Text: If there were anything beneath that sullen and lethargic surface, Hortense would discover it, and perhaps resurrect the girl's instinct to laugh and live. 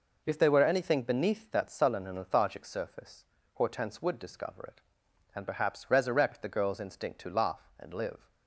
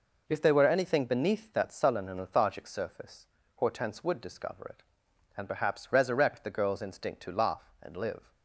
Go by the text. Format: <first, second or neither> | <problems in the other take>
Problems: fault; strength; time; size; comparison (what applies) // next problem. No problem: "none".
neither | none